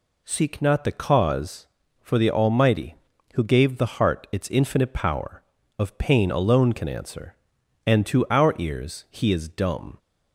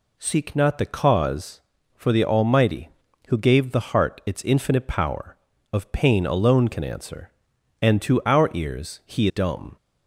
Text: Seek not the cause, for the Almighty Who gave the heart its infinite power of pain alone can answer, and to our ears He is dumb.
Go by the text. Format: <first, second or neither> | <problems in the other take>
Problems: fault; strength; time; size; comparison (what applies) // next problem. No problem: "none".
first | skips "is"; at 9.2 s